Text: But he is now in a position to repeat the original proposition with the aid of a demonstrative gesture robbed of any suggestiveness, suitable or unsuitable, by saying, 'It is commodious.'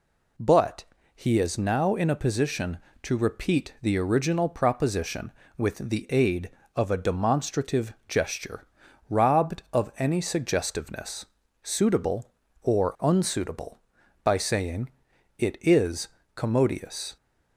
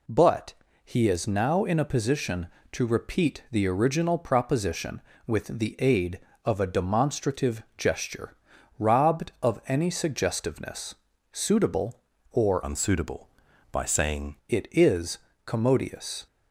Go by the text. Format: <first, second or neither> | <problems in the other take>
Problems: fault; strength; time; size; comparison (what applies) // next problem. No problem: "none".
first | pauses between "But" and "he"; slight; at 0.5 s; 0.30 s long; slight in the first // pauses between "demonstrative" and "gesture"; slight; at 7.6 s; 0.16 s long; slight in the first // pauses between "gesture" and "robbed"; at 8.3 s; 0.44 s long; also in the first // changes voice from "unsuitable" to "saying"; from 12.6 to 14.3 s; 1.7 s long // pauses between "is" and "commodious"; slight; at 15.1 s; 0.26 s long; slight in the first